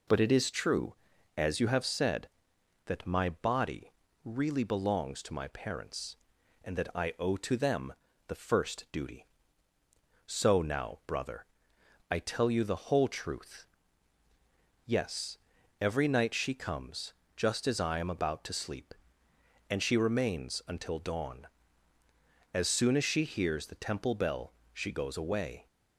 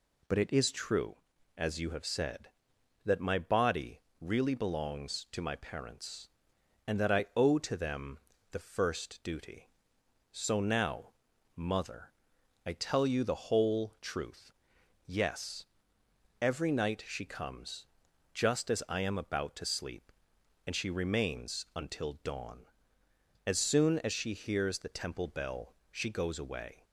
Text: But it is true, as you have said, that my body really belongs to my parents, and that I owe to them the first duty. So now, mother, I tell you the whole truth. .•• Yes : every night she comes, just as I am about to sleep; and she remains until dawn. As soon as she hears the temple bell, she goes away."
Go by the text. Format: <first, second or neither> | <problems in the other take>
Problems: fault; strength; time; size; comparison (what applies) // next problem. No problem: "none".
second | pauses between "body" and "really"; slight; at 3.9 s; 0.32 s long; slight in the second // pauses between "them" and "the"; slight; at 7.9 s; 0.34 s long; slight in the second // says "brother" for "mother"; at 11.0 s